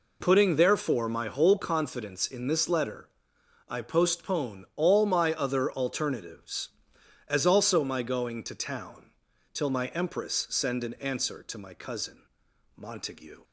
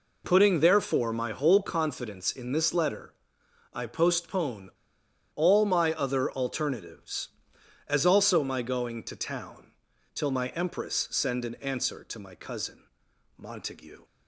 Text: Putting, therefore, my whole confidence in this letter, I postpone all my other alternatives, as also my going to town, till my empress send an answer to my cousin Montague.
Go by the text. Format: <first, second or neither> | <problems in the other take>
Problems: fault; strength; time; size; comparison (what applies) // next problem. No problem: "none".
first | pauses between "postpone" and "all"; noticeable; at 4.6 s; 0.64 s long // pauses between "cousin" and "Montague"; noticeable; at 12.8 s; 0.52 s long; noticeable in the first